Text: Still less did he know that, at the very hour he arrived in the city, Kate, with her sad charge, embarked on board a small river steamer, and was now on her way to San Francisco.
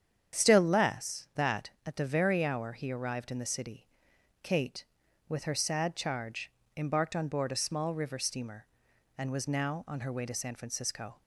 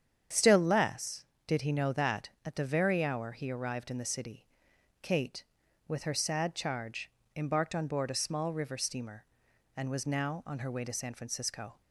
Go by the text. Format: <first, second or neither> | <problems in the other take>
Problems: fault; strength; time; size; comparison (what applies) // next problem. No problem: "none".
second | starts louder than the rest; strong; until 1.4 s; 8.5 dB; strong in the second // skips "did he know"; at 1.3 s